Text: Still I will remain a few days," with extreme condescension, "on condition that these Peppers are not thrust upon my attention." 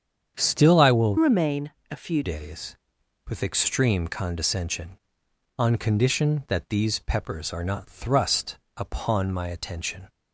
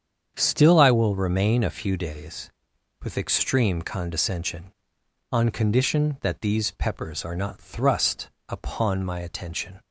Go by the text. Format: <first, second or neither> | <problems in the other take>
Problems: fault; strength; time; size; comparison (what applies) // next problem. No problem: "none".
second | starts louder than the rest; strong; until 1.3 s; 8 dB; strong in the second // changes voice from "remain" to "few"; from 1.1 to 2.2 s; 1.1 s long // pauses between "remain" and "a"; slight; at 1.7 s; 0.20 s long // pauses between "thrust" and "upon"; slight; at 8.5 s; 0.18 s long; slight in the second